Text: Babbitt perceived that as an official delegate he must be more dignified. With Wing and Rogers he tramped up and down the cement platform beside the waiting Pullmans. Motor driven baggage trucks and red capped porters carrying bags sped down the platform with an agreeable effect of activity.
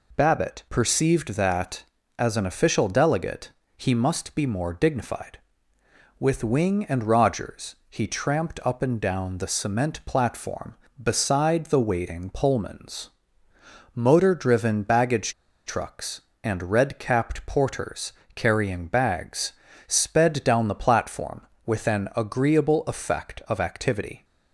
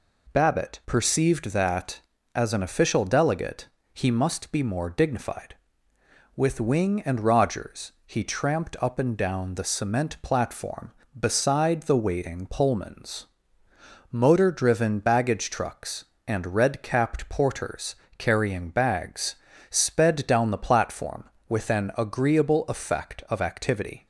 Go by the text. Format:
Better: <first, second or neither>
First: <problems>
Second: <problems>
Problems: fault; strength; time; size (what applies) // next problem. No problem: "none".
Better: second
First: pauses between "delegate" and "he"; slight; at 3.5 s; 0.26 s long // pauses between "baggage" and "trucks"; slight; at 15.3 s; 0.33 s long // pauses between "porters" and "carrying"; slight; at 18.1 s; 0.22 s long // pauses between "bags" and "sped"; slight; at 19.5 s; 0.34 s long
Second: pauses between "delegate" and "he"; slight; at 3.6 s; 0.26 s long // pauses between "porters" and "carrying"; slight; at 17.9 s; 0.22 s long // pauses between "bags" and "sped"; slight; at 19.3 s; 0.34 s long